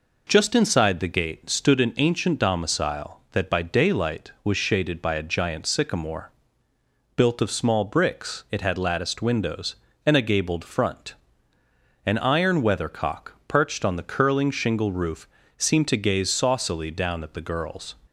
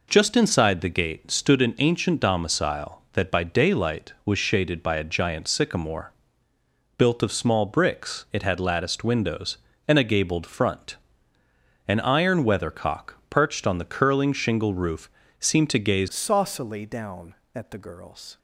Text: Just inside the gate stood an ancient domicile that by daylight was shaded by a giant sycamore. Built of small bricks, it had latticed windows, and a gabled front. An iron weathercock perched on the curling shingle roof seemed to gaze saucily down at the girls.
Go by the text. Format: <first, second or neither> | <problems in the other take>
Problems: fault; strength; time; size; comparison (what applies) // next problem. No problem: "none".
first | pauses between "roof" and "seemed"; slight; at 15.1 s; 0.28 s long; slight in the first // changes voice at "saucily"; from 16.0 s on; 2.3 s long